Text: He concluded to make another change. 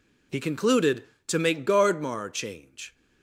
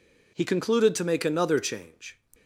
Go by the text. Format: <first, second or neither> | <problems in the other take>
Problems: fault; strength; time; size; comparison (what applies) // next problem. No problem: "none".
second | says "gardmar" for "another"; at 1.6 s